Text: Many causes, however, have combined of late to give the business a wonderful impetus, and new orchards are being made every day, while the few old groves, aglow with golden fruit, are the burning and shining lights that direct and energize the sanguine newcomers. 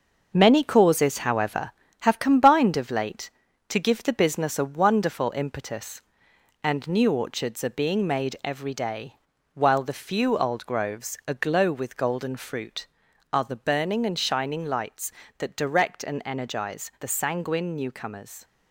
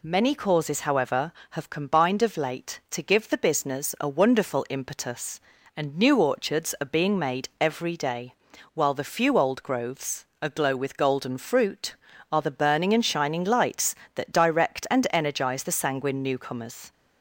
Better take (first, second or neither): second